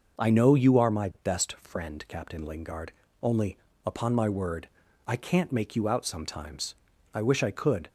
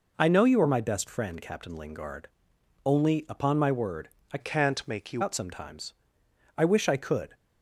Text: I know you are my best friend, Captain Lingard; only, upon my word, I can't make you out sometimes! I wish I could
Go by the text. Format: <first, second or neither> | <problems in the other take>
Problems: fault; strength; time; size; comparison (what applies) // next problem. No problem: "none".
first | changes voice from "can't" to "you"; from 4.3 to 5.2 s; 0.9 s long